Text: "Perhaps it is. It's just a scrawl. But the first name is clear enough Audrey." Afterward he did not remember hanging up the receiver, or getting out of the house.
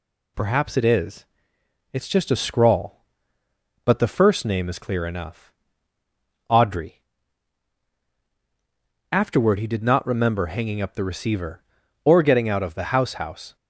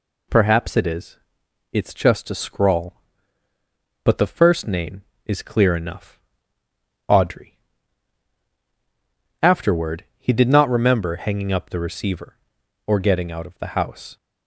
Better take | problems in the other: second | pauses between "enough" and "Audrey"; noticeable; at 5.5 s; 0.96 s long; noticeable in the second // says "house" twice; at 13.1 s

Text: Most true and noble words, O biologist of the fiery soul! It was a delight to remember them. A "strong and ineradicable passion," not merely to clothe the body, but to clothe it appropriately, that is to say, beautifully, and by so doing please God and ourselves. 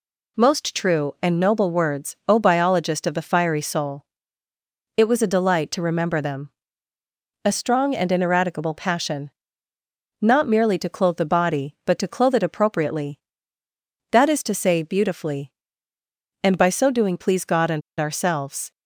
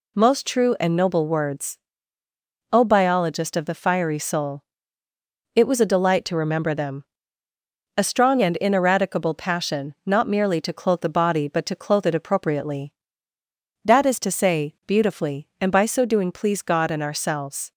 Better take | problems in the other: second | pauses between "and" and "ourselves"; slight; at 17.8 s; 0.19 s long

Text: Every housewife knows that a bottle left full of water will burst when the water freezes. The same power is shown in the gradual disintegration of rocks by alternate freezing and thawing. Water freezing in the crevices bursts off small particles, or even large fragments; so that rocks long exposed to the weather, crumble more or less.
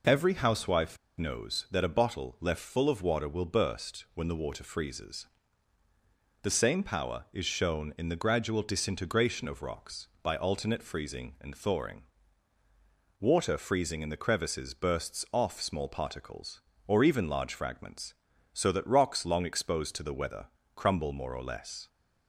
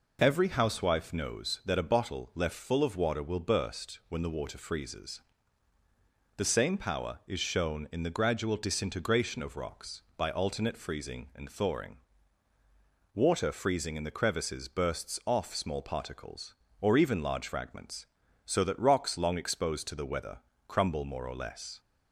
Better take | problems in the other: second | pauses between "housewife" and "knows"; slight; at 0.9 s; 0.22 s long

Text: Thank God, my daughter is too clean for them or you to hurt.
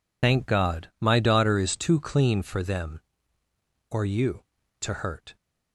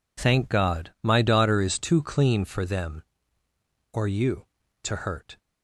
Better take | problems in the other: second | loses the start of "Thank"; at 0.2 s; 80 ms

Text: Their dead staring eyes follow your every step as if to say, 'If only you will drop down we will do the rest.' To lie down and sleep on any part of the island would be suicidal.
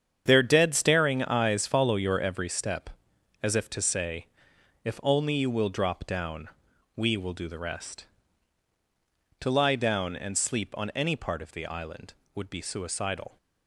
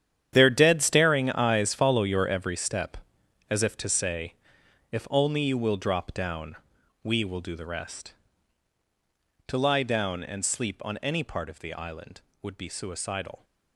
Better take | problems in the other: first | gets quieter; strong; throughout; 14 dB // starts louder than the rest; strong; until 1.3 s; 9.5 dB; strong in the first // pauses between "down" and "we"; noticeable; at 6.5 s; 0.48 s long; noticeable in the first

